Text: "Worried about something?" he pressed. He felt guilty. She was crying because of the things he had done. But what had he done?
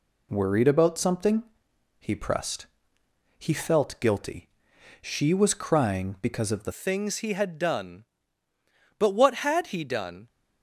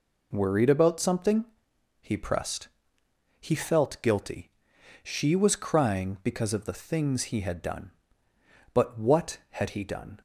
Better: second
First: changes voice at "things"; from 6.7 s on; 3.5 s long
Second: none

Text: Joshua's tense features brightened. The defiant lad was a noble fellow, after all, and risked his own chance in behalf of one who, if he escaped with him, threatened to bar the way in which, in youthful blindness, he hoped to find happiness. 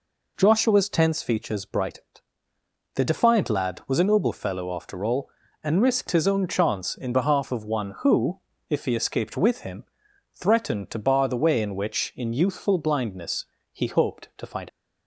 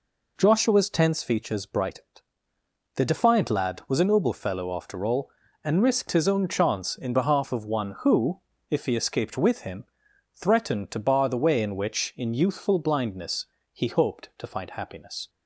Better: second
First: stops before "happiness"; at 14.6 s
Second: none

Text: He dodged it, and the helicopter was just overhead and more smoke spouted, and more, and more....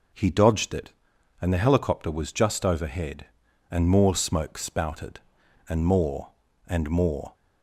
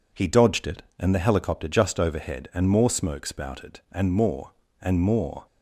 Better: first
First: none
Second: skips "was"; at 1.6 s

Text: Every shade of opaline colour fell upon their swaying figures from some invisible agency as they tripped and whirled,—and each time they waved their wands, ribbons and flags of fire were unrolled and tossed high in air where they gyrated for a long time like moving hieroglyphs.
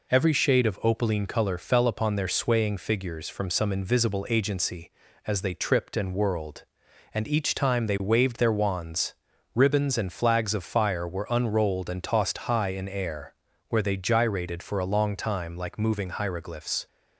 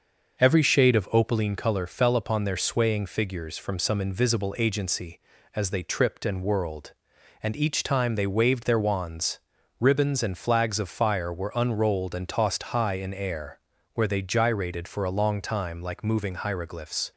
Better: first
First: pauses between "air" and "where"; slight; at 13.3 s; 0.36 s long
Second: starts louder than the rest; until 1.3 s; 6 dB // pauses between "air" and "where"; slight; at 13.5 s; 0.36 s long

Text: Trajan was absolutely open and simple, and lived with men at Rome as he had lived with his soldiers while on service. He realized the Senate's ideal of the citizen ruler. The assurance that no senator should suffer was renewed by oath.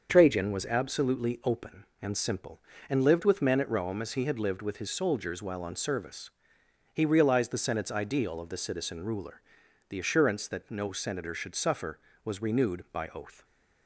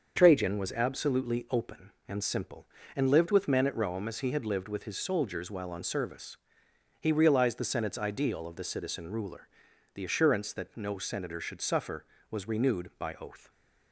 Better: neither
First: starts louder than the rest; until 1.1 s; 6.5 dB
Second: starts louder than the rest; until 1.1 s; 6.5 dB

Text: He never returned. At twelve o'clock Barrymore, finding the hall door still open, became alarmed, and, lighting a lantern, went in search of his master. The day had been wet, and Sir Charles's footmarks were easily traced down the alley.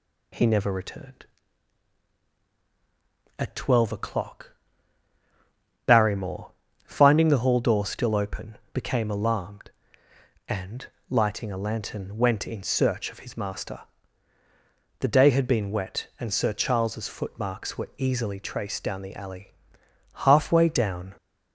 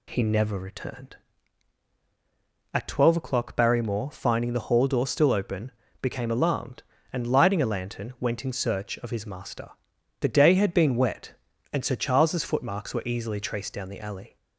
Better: second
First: pauses between "o'clock" and "Barrymore"; strong; at 4.5 s; 1.3 s long // goes on to say "Halfway down"; noticeable; from 20.1 s on; 1.0 s long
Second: none

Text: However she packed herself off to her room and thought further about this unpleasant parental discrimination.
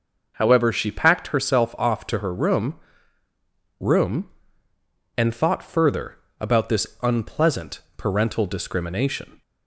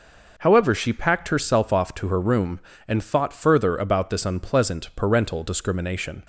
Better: second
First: says "room" twice; at 3.7 s // pauses between "further" and "about"; slight; at 6.1 s; 0.22 s long // pauses between "this" and "unpleasant"; slight; at 6.8 s; 0.16 s long // pauses between "unpleasant" and "parental"; slight; at 7.7 s; 0.18 s long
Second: none

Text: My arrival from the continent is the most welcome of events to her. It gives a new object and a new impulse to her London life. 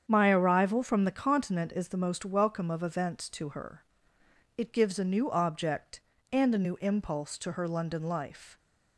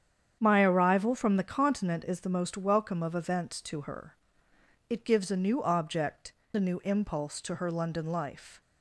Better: first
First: starts louder than the rest; strong; until 1.0 s; 8 dB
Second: starts louder than the rest; strong; until 1.4 s; 8.5 dB // skips "and"; at 6.4 s

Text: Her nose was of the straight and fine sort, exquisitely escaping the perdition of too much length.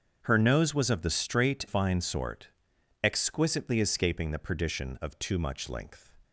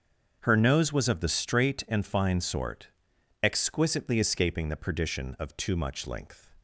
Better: second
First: starts louder than the rest; strong; until 1.2 s; 7.5 dB // skips "and"; at 1.6 s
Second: starts louder than the rest; strong; until 1.4 s; 7 dB

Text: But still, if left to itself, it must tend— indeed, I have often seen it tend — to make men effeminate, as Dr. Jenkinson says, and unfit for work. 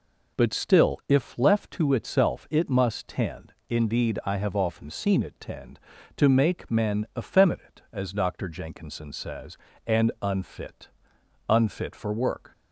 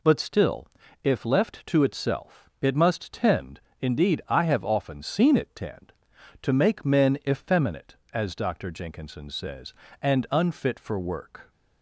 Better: second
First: says "unfit" twice; at 11.4 s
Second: none

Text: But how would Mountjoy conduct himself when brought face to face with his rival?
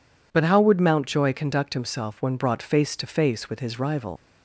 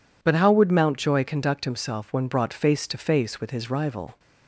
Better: second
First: leaves "rival" unfinished; at 4.1 s; 115 ms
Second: none

